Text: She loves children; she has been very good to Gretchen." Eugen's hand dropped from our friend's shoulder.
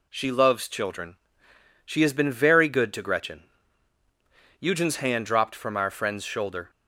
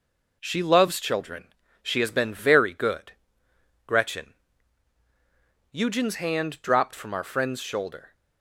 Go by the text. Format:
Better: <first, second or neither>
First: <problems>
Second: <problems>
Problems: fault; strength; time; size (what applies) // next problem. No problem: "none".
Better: first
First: none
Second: skips "to"; at 3.4 s